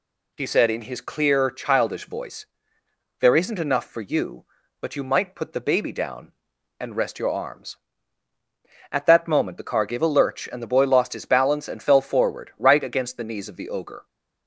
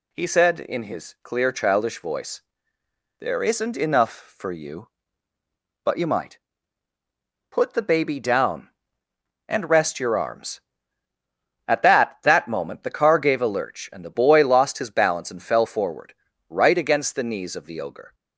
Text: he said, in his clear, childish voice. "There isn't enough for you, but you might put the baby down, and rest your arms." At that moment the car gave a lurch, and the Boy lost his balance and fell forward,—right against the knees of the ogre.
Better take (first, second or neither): first